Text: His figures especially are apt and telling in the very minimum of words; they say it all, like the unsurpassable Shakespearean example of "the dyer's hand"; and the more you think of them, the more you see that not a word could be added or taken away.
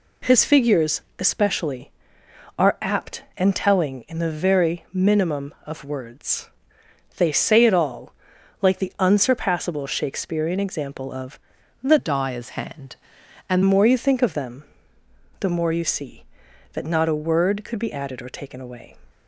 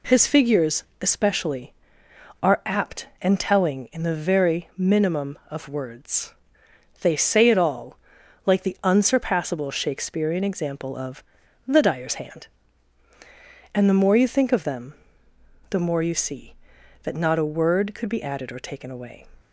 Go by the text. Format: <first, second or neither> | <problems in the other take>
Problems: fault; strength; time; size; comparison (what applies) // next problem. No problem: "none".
second | pauses between "figures" and "especially"; slight; at 1.0 s; 0.18 s long; slight in the second // pauses between "of" and "the"; at 11.3 s; 0.44 s long; also in the second // changes voice from "dyer's" to "and"; from 11.9 to 13.6 s; 1.7 s long